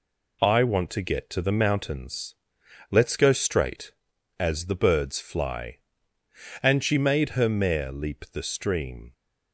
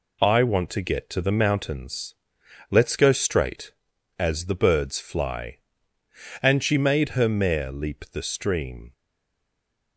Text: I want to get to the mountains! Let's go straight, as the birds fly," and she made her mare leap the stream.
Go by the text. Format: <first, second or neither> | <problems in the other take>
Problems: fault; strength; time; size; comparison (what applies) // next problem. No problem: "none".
first | stays silent after the last word; from 8.9 s on; 1.0 s long